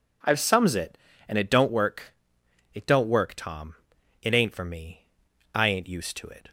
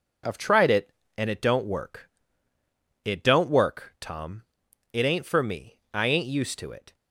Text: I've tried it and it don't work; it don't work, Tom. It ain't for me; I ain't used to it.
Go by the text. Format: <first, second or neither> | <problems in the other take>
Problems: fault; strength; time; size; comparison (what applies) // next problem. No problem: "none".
second | says "sums" for "tried"; at 0.3 s